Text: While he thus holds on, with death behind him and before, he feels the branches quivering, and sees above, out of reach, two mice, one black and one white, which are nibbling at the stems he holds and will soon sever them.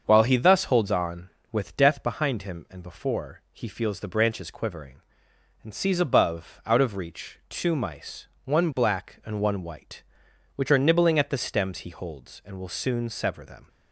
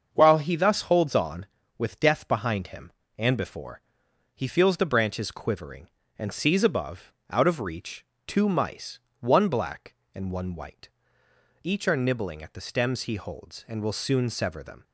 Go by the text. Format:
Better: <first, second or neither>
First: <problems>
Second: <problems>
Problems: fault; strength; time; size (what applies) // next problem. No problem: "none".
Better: first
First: starts louder than the rest; until 1.0 s; 6.5 dB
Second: starts louder than the rest; until 1.1 s; 6.5 dB // says "each" for "which"; at 11.6 s